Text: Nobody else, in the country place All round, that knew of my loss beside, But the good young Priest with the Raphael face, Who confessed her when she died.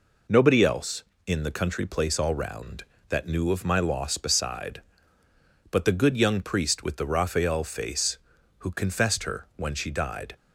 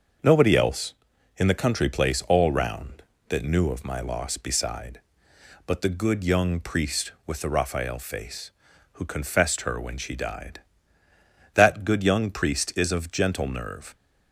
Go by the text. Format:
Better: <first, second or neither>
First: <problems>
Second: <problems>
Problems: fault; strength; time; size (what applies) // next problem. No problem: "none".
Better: first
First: none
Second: starts louder than the rest; until 1.6 s; 6.5 dB // goes on to say "That good young Priest is of gentle nerve"; strong; from 11.5 s on; 2.4 s long